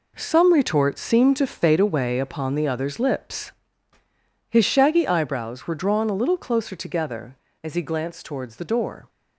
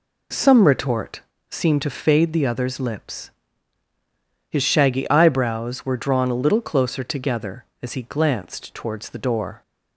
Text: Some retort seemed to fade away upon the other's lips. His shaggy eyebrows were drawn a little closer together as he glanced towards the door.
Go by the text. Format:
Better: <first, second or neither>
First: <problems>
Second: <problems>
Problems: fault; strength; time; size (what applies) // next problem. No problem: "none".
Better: first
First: none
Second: pauses between "retort" and "seemed"; slight; at 1.1 s; 0.30 s long // skips "away upon"; at 2.3 s